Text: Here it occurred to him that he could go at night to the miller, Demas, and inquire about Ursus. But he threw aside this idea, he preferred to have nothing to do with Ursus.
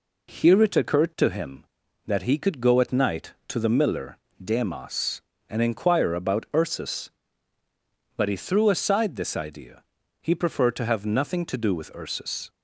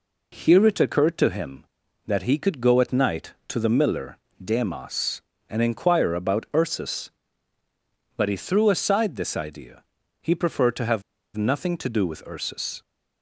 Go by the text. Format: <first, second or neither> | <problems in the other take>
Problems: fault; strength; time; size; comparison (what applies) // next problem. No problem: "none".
first | pauses between "have" and "nothing"; slight; at 11.0 s; 0.34 s long